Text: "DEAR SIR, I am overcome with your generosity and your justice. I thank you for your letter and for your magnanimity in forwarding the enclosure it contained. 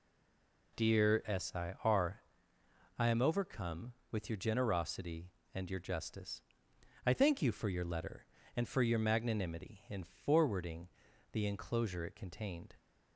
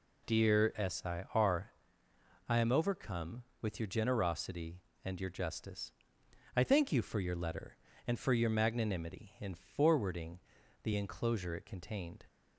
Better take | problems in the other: second | stays silent before the first word; slight; until 0.7 s; 0.7 s long // pauses between "forwarding" and "the"; at 10.8 s; 0.44 s long; also in the second

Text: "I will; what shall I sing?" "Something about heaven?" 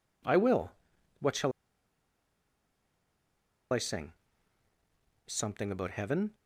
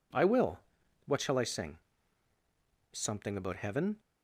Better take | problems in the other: second | pauses between "shall" and "I"; strong; at 1.5 s; 2.2 s long

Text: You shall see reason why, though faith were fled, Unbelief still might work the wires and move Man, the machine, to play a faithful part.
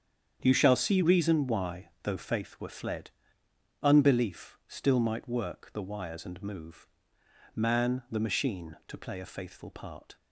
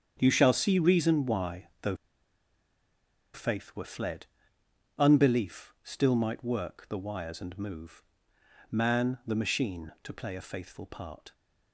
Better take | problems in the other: first | starts louder than the rest; strong; until 1.2 s; 8 dB; strong in the first // pauses between "though" and "faith"; strong; at 1.9 s; 1.3 s long // pauses between "move" and "Man"; noticeable; at 8.0 s; 0.68 s long; noticeable in the first

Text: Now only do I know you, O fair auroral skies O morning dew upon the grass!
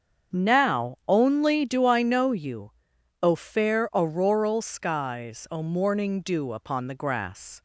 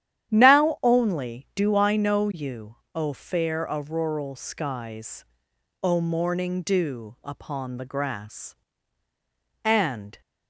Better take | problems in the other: first | starts louder than the rest; strong; until 1.3 s; 10.5 dB; strong in the first // pauses between "skies" and "O"; noticeable; at 5.2 s; 0.58 s long // goes on to say "And"; from 9.6 s on; 0.56 s long

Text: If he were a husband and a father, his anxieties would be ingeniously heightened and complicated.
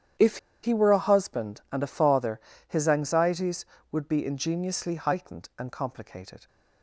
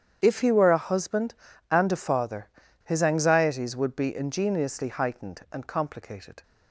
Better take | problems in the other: second | starts louder than the rest; strong; until 1.4 s; 9.5 dB; strong in the second // pauses between "If" and "he"; slight; at 0.3 s; 0.26 s long

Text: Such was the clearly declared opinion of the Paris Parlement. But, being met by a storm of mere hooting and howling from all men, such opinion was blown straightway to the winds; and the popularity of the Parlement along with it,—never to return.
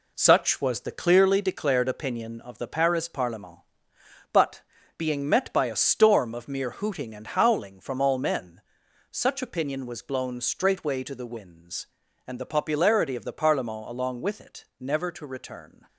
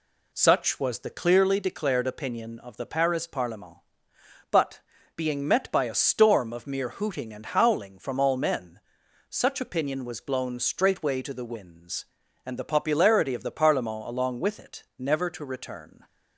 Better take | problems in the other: second | gets quieter; throughout; 7 dB

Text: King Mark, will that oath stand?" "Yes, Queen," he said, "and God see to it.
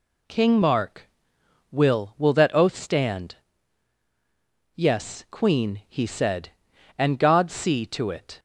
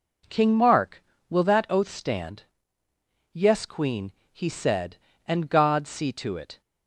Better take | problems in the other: second | says "will" twice; at 2.1 s

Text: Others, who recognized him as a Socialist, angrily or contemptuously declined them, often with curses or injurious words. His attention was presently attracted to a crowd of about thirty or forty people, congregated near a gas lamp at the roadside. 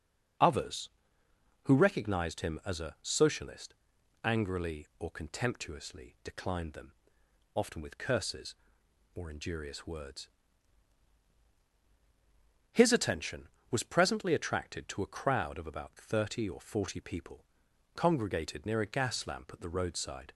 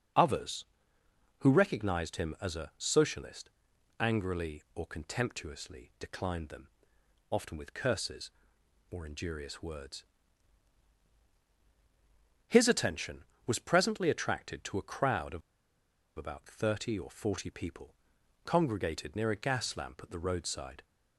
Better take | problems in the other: first | starts louder than the rest; until 1.9 s; 7 dB; also in the first // pauses between "of" and "about"; noticeable; at 15.4 s; 0.75 s long

